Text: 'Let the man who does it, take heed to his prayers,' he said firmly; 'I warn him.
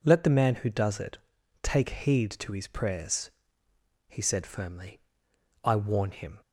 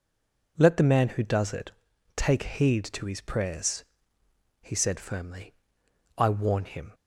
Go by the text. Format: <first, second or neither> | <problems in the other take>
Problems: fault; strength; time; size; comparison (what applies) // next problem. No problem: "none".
first | stays silent before the first word; slight; until 0.5 s; 0.5 s long